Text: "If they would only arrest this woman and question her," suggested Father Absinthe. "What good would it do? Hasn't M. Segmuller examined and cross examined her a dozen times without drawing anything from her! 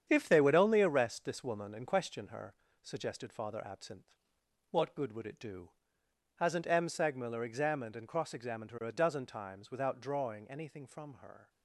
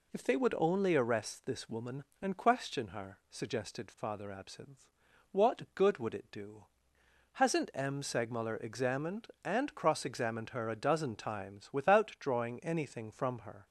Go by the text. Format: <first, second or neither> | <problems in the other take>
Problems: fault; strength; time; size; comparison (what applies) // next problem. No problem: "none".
second | gets quieter; strong; throughout; 7.5 dB